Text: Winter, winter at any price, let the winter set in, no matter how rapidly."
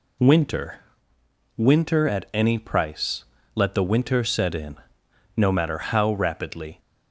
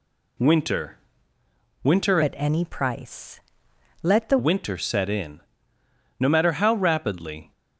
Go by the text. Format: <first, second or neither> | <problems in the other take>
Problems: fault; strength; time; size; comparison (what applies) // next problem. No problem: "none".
first | changes voice from "at" to "the"; from 2.2 to 4.3 s; 2.1 s long